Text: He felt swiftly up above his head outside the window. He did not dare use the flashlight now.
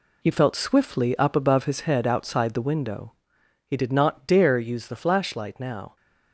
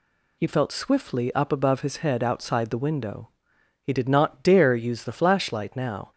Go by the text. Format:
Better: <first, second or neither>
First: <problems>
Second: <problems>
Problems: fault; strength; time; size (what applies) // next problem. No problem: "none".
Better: second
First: gets quieter; strong; throughout; 9 dB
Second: none